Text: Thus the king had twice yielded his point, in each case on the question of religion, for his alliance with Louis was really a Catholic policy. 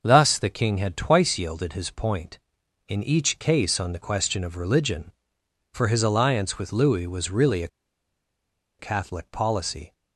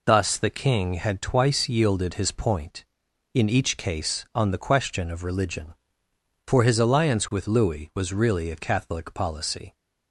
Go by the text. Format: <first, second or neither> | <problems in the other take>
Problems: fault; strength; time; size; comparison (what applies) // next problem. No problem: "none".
second | starts louder than the rest; noticeable; until 1.0 s; 6 dB // pauses between "a" and "Catholic"; at 7.6 s; 1.1 s long